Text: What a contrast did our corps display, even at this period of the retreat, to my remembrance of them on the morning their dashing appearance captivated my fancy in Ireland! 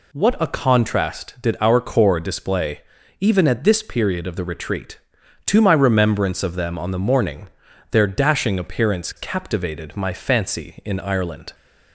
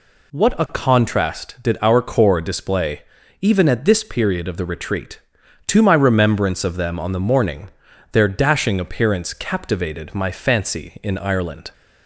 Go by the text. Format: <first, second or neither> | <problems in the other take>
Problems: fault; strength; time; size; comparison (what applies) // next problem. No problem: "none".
neither | pauses between "morning" and "their"; the same in both